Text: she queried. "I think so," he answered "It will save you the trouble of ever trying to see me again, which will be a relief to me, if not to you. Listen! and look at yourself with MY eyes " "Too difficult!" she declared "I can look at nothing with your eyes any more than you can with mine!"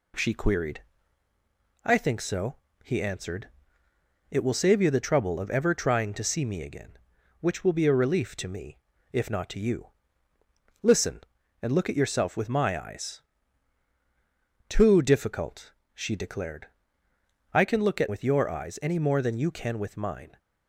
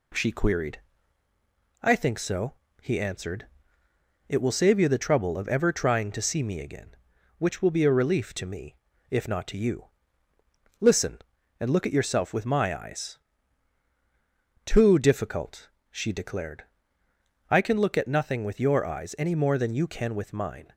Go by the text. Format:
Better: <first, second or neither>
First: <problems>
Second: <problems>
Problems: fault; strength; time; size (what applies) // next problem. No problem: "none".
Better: second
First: pauses between "answered" and "It"; noticeable; at 3.4 s; 0.82 s long // pauses between "declared" and "I"; noticeable; at 16.6 s; 0.88 s long // skips "nothing"; at 18.0 s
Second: pauses between "answered" and "It"; noticeable; at 3.4 s; 0.82 s long // pauses between "declared" and "I"; noticeable; at 16.6 s; 0.88 s long